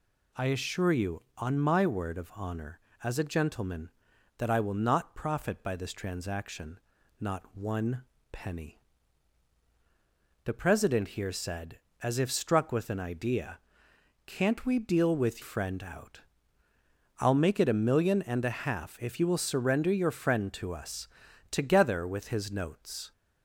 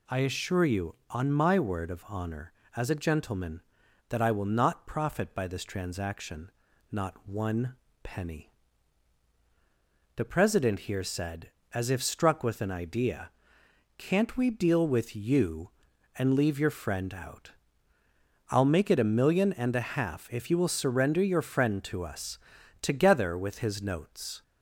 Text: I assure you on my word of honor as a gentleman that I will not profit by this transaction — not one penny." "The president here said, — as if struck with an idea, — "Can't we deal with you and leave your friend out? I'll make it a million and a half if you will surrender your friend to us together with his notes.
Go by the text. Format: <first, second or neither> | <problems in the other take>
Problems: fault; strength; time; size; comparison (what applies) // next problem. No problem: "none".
second | pauses between "one" and "penny"; slight; at 8.0 s; 0.26 s long; slight in the second // skips "you and leave your"; at 15.4 s // pauses between "us" and "together"; at 21.0 s; 0.44 s long; also in the second